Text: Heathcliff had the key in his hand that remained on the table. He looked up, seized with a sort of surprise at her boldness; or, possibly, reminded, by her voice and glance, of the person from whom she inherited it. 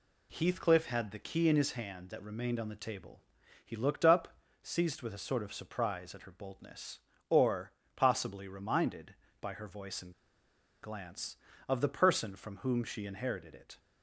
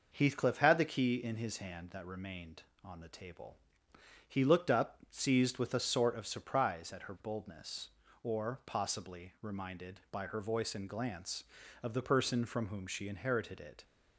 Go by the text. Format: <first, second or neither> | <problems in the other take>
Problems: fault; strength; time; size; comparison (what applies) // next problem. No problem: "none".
second | pauses between "and" and "glance"; noticeable; at 10.1 s; 0.70 s long